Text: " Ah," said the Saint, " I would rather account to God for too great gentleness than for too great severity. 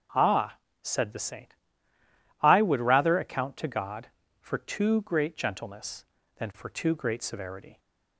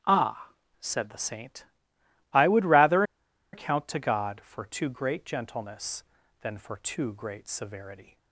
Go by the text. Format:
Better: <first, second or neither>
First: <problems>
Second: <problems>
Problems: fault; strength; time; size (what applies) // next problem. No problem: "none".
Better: first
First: starts louder than the rest; strong; until 1.3 s; 7 dB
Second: starts louder than the rest; strong; until 1.2 s; 9 dB // pauses between "rather" and "account"; noticeable; at 3.0 s; 0.50 s long